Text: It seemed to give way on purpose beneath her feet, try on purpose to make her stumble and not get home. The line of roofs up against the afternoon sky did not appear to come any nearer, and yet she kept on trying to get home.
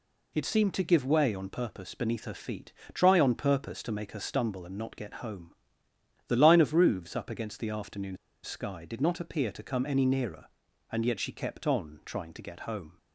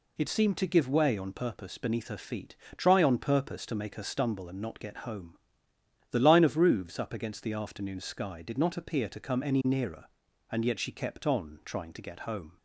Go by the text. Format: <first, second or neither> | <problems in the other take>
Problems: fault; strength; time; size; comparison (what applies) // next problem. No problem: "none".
second | pauses between "afternoon" and "sky"; slight; at 8.1 s; 0.26 s long